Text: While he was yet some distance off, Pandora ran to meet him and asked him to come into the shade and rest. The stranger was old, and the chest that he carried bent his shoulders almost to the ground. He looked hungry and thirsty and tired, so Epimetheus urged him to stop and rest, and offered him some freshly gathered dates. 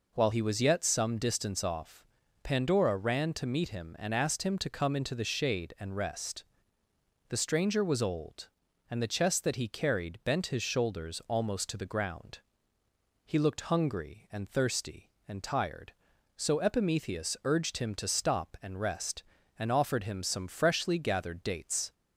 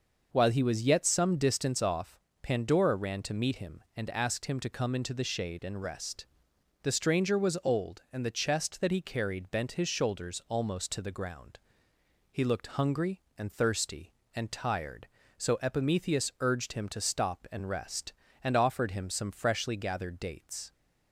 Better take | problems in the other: neither | none

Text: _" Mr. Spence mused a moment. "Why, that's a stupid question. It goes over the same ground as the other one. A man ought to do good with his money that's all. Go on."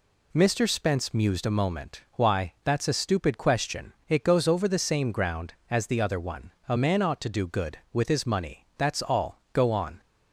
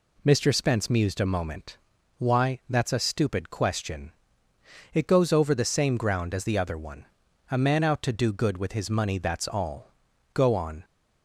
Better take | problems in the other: first | says "out" for "ought"; at 7.8 s

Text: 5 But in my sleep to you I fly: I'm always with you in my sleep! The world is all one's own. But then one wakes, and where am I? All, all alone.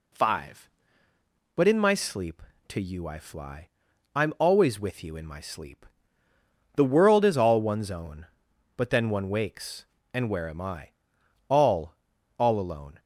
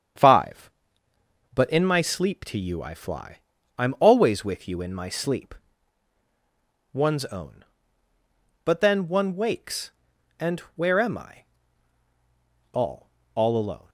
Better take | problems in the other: first | starts louder than the rest; strong; until 1.9 s; 8 dB // skips "The world is all"; at 6.2 s // pauses between "and" and "where"; slight; at 10.5 s; 0.16 s long

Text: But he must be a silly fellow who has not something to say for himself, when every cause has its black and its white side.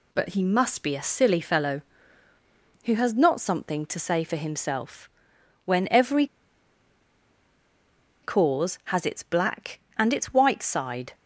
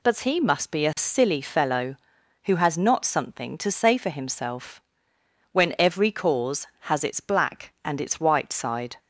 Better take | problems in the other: second | pauses between "every" and "cause"; strong; at 6.2 s; 1.9 s long

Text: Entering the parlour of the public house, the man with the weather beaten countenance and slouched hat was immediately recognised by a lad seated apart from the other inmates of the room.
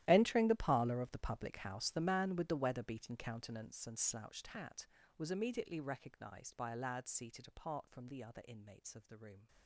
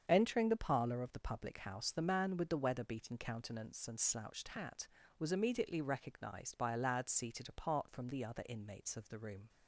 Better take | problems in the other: second | gets quieter; strong; throughout; 19 dB // starts louder than the rest; strong; until 1.0 s; 13.5 dB; strong in the second

